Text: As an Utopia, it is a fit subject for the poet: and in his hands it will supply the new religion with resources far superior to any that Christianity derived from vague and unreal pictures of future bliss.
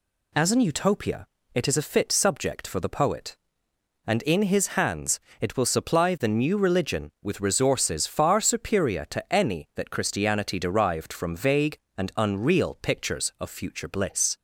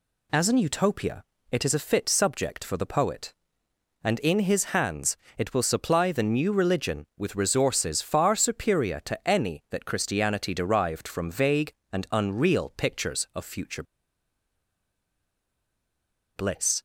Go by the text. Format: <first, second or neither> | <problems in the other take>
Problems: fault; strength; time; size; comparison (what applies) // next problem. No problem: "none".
first | pauses between "hands" and "it"; slight; at 5.1 s; 0.20 s long; slight in the first // pauses between "future" and "bliss"; strong; at 13.8 s; 2.5 s long